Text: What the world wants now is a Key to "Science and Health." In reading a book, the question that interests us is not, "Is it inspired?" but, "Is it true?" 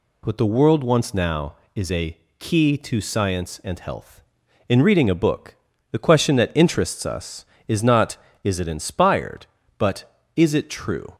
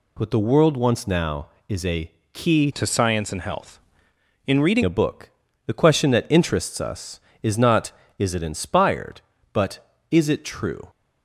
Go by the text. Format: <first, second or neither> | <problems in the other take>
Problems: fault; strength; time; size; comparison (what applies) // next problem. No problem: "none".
first | pauses between "a" and "Key"; slight; at 2.1 s; 0.22 s long; slight in the first // changes voice from "to" to "reading"; from 2.7 to 4.8 s; 2.1 s long